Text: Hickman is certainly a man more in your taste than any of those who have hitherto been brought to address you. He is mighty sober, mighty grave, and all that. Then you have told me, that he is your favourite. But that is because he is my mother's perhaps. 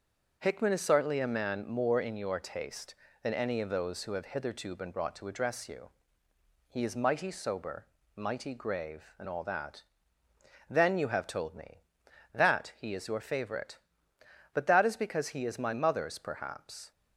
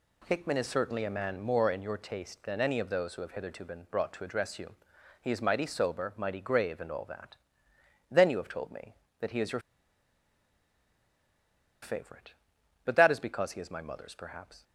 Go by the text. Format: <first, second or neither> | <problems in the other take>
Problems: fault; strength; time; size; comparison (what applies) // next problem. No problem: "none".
first | pauses between "your" and "favourite"; strong; at 9.6 s; 2.2 s long